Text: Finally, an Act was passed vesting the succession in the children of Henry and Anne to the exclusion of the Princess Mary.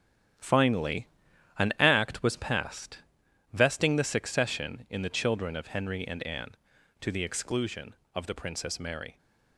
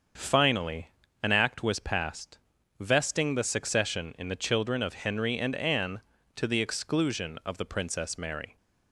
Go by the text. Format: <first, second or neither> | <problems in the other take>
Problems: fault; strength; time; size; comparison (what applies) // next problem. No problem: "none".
second | gets quieter; strong; throughout; 8.5 dB // starts louder than the rest; strong; until 1.9 s; 10.5 dB; also in the second // pauses between "passed" and "vesting"; noticeable; at 2.9 s; 0.54 s long; also in the second